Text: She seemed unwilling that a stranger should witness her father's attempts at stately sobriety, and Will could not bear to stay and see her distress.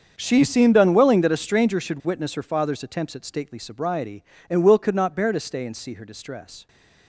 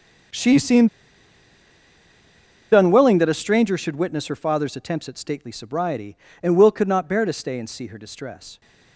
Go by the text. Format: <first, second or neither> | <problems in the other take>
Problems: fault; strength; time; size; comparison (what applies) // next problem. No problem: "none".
first | starts louder than the rest; until 3.1 s; 7 dB; also in the first // pauses between "seemed" and "unwilling"; strong; at 0.8 s; 1.8 s long